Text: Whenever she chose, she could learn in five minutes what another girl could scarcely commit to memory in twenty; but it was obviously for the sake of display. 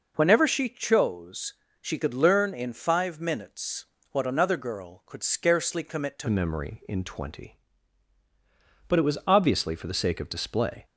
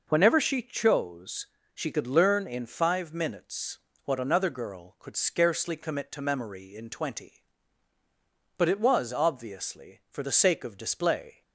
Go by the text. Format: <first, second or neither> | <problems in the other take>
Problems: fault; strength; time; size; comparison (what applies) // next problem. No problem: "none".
second | pauses between "minutes" and "what"; slight; at 3.8 s; 0.28 s long; slight in the second // changes voice at "memory"; from 6.2 s on; 4.6 s long